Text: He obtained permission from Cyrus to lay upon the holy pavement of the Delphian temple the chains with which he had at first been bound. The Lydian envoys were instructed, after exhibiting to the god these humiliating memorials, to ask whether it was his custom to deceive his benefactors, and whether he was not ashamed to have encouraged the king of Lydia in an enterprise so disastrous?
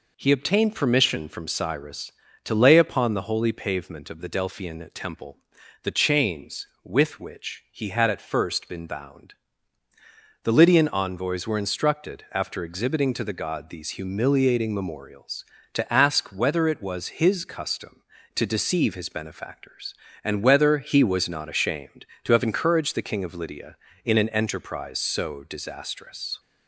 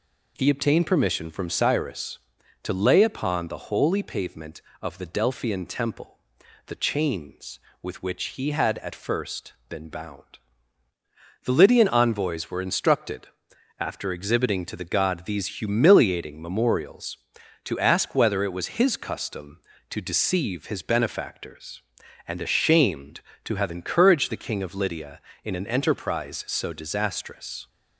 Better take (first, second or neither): first